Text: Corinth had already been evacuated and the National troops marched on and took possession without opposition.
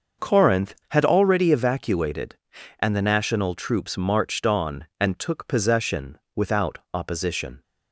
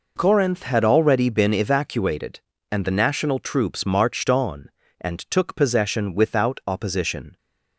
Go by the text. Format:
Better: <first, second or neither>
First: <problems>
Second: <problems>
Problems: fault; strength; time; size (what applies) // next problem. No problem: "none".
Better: second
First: starts louder than the rest; until 1.3 s; 6.5 dB // skips "been"; at 1.5 s // pauses between "possession" and "without"; slight; at 6.1 s; 0.16 s long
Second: none